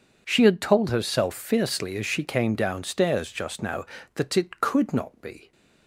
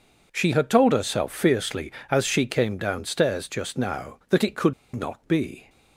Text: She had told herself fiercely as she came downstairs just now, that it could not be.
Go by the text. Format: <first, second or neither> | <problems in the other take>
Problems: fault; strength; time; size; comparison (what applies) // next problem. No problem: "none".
first | pauses between "could" and "not"; slight; at 4.7 s; 0.21 s long